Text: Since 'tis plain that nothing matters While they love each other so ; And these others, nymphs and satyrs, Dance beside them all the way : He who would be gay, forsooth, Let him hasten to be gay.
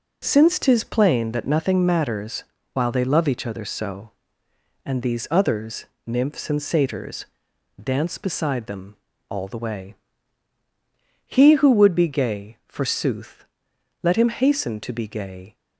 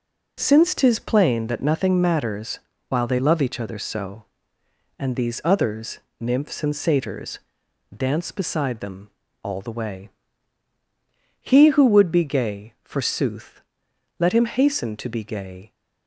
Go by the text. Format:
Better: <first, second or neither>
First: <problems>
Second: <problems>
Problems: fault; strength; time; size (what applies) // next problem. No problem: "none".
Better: neither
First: pauses between "matters" and "While"; slight; at 2.4 s; 0.26 s long // pauses between "them" and "all"; slight; at 8.9 s; 0.32 s long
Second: pauses between "matters" and "While"; slight; at 2.6 s; 0.26 s long // pauses between "them" and "all"; slight; at 9.0 s; 0.32 s long